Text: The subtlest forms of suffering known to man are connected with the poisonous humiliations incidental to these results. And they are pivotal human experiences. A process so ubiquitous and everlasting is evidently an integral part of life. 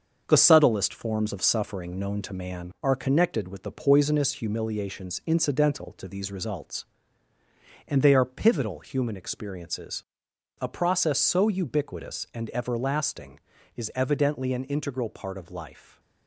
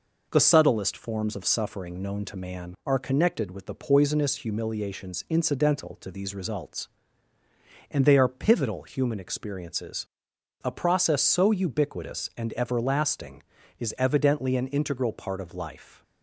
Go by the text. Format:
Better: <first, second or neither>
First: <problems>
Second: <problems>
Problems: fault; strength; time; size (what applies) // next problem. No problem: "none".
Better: second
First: gets quieter; noticeable; throughout; 6 dB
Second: none